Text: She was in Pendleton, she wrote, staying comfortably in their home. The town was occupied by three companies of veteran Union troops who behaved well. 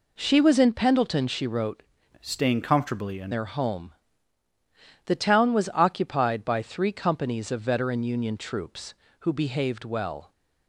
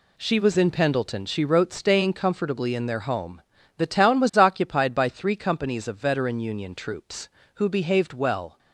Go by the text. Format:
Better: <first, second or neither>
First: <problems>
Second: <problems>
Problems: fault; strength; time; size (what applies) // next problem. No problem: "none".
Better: second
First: changes voice from "staying" to "in"; from 2.2 to 3.3 s; 1.1 s long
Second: none